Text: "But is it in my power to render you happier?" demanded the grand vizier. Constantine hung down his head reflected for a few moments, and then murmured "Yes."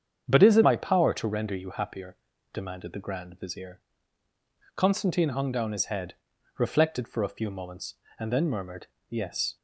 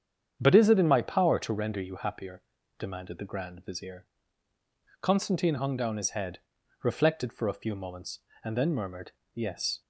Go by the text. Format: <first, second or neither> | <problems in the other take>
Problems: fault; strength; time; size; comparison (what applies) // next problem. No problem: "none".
second | starts louder than the rest; strong; until 1.3 s; 8 dB; strong in the second // skips "in"; at 0.6 s // pauses between "head" and "reflected"; at 6.1 s; 0.44 s long; also in the second // pauses between "murmured" and "Yes"; slight; at 8.8 s; 0.22 s long; slight in the second